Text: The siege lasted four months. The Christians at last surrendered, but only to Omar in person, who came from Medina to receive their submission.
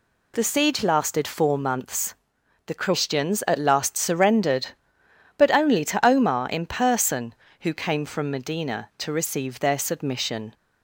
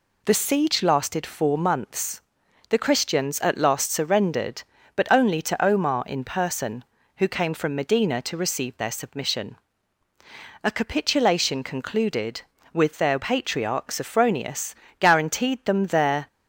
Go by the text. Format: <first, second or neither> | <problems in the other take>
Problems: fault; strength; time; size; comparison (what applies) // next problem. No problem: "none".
first | goes on to say "A capitulation concluded with their patriarch Sophronius guaranteed them their"; strong; from 10.6 s on; 5.6 s long